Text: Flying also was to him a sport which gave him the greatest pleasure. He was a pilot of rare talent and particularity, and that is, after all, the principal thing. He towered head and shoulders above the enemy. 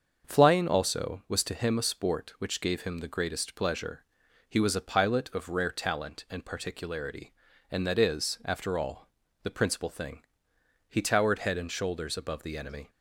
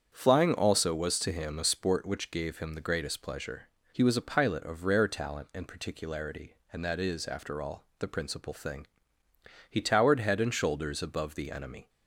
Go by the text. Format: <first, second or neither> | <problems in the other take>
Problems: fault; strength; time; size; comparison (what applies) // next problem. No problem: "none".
neither | starts louder than the rest; the same in both